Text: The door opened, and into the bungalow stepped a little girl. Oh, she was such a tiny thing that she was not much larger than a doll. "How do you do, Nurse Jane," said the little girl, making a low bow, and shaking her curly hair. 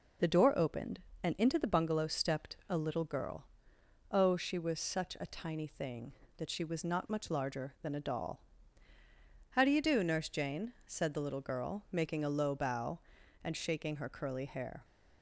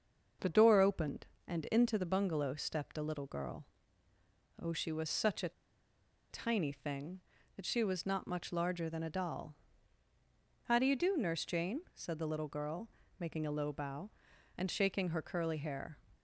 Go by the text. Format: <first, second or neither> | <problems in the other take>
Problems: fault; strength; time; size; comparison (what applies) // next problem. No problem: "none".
first | starts louder than the rest; until 1.5 s; 6 dB // pauses between "a" and "tiny"; noticeable; at 5.5 s; 0.79 s long